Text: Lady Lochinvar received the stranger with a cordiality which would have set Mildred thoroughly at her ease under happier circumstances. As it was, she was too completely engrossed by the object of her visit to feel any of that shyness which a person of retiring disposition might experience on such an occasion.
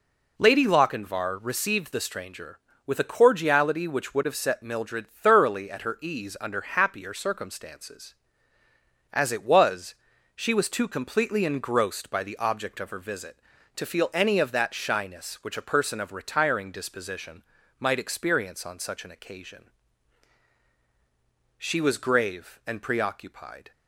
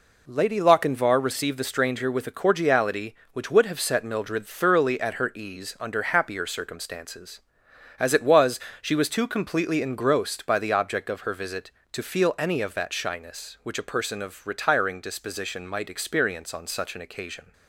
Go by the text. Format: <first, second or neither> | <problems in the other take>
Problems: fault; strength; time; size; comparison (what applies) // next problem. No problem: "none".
second | pauses between "disposition" and "might"; slight; at 17.4 s; 0.36 s long // goes on to say "She was grave and preoccupied"; strong; from 21.5 s on; 2.1 s long